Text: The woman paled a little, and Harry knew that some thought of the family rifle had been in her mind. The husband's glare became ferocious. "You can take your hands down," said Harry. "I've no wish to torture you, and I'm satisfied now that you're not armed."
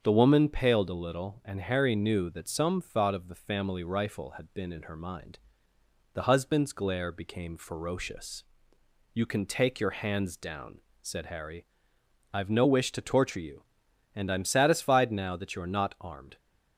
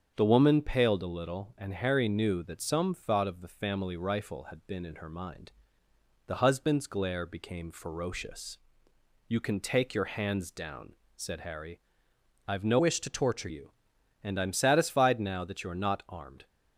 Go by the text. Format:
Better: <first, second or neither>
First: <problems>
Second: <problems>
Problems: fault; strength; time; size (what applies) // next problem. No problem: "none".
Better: first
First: starts louder than the rest; strong; until 1.0 s; 7.5 dB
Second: starts louder than the rest; strong; until 1.1 s; 7.5 dB // changes voice from "wish" to "torture"; from 12.7 to 13.4 s; 0.7 s long